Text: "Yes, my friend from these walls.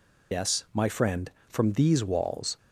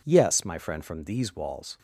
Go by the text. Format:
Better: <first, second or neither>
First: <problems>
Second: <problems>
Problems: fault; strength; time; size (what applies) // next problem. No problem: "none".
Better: second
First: loses the start of "Yes"; at 0.3 s; 105 ms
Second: none